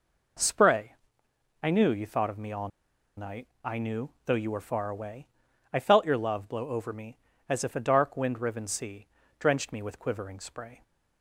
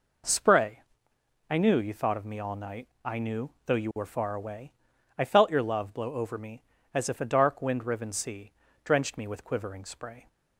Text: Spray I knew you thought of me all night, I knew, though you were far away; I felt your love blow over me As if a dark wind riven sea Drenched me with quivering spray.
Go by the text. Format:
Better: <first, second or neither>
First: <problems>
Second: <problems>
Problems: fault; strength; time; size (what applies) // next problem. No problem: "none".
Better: second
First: pauses between "Spray" and "I"; noticeable; at 0.9 s; 0.70 s long // pauses between "all" and "night"; noticeable; at 2.6 s; 0.49 s long // pauses between "sea" and "Drenched"; slight; at 9.0 s; 0.32 s long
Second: pauses between "Spray" and "I"; noticeable; at 0.8 s; 0.70 s long // pauses between "sea" and "Drenched"; slight; at 8.5 s; 0.32 s long